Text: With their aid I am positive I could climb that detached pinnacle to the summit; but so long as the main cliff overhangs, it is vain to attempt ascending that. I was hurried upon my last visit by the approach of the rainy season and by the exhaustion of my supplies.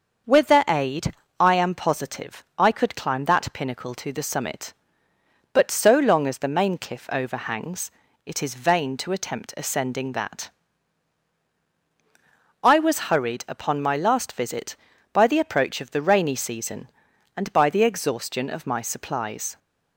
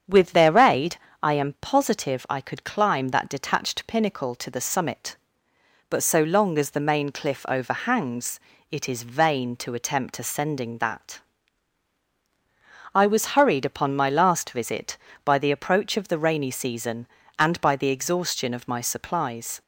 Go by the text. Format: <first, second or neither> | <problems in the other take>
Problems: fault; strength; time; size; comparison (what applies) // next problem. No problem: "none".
second | starts louder than the rest; until 1.5 s; 6.5 dB; strong in the second // pauses between "aid" and "I"; slight; at 1.1 s; 0.24 s long; slight in the second // skips "detached"; at 3.5 s